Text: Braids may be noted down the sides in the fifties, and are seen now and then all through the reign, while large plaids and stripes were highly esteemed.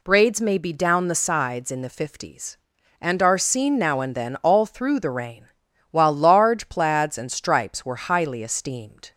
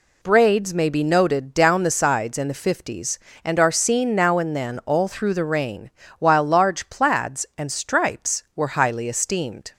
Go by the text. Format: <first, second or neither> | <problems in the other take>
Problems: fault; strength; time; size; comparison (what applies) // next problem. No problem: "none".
second | skips "noted"; at 0.7 s